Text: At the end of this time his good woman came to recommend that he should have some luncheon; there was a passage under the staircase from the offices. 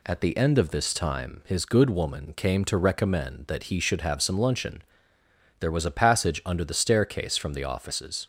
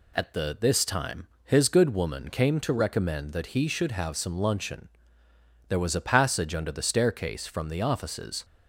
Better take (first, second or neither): first